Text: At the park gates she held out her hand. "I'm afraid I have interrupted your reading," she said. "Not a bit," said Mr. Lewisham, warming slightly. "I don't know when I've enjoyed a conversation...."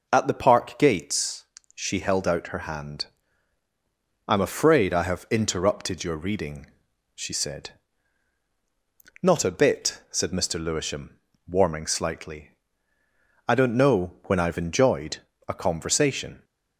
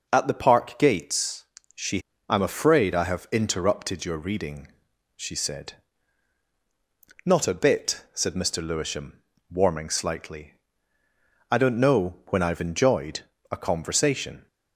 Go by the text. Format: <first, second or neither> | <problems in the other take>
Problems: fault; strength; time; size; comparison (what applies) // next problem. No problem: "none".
first | pauses between "gates" and "she"; slight; at 1.4 s; 0.32 s long; slight in the first // skips "held out her hand"; at 2.1 s // pauses between "enjoyed" and "a"; slight; at 13.2 s; 0.30 s long; slight in the first